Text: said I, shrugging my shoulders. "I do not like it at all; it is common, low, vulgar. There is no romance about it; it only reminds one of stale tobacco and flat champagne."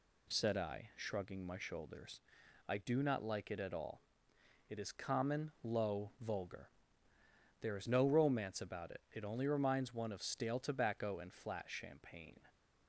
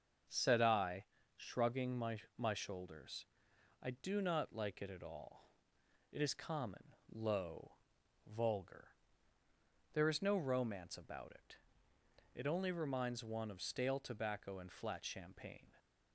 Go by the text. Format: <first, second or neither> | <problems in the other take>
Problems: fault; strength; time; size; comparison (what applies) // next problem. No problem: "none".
first | starts louder than the rest; until 1.6 s; 6.5 dB // says "my" twice; at 2.3 s